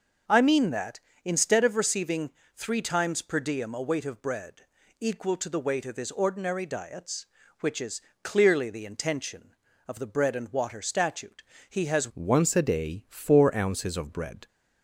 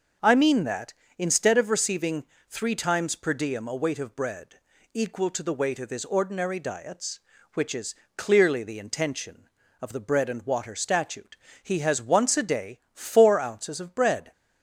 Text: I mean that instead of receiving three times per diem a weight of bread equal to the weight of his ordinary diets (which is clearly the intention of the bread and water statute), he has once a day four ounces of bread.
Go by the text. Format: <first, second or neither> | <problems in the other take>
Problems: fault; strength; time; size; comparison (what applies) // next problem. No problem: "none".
second | starts louder than the rest; noticeable; until 1.5 s; 6 dB; also in the second // pauses between "receiving" and "three"; slight; at 2.2 s; 0.26 s long; slight in the second // pauses between "bread" and "equal"; at 4.6 s; 0.38 s long; also in the second // pauses between "is" and "clearly"; slight; at 7.9 s; 0.22 s long; slight in the second // changes voice at "once"; from 12.1 s on; 2.3 s long